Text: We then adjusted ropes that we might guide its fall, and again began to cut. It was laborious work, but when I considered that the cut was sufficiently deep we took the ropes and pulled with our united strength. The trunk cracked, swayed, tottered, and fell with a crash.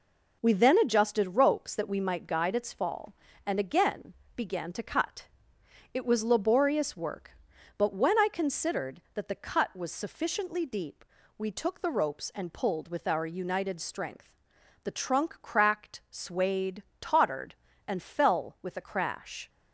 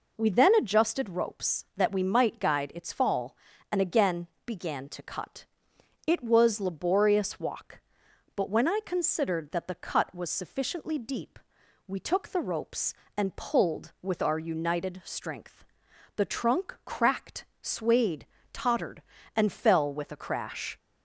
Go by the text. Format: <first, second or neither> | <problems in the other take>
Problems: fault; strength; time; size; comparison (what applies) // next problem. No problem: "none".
first | pauses between "again" and "began"; slight; at 4.2 s; 0.20 s long; slight in the first // says "walk" for "work"; at 7.3 s // pauses between "deep" and "we"; noticeable; at 11.3 s; 0.50 s long; slight in the first